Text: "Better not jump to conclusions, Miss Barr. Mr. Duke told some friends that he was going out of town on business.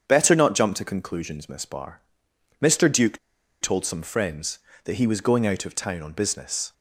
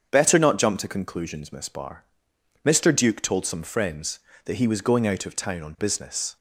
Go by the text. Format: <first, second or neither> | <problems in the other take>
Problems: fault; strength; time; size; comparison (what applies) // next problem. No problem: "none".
second | starts louder than the rest; strong; until 1.0 s; 7 dB; strong in the second // pauses between "Duke" and "told"; at 3.1 s; 0.43 s long